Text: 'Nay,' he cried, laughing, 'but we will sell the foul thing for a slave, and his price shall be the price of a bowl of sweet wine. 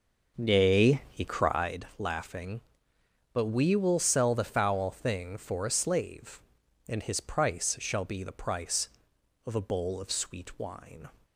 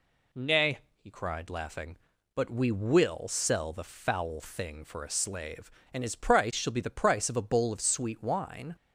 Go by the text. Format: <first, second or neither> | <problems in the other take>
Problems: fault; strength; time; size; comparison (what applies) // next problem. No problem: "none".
second | starts louder than the rest; noticeable; until 1.8 s; 6 dB